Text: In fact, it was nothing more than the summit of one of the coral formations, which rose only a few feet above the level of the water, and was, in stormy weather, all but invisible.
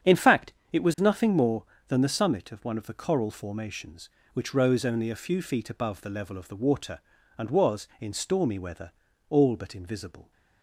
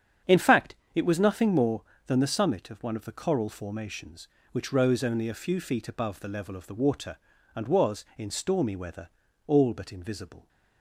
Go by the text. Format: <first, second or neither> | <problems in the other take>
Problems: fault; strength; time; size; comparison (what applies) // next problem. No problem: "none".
neither | starts louder than the rest; strong; the same in both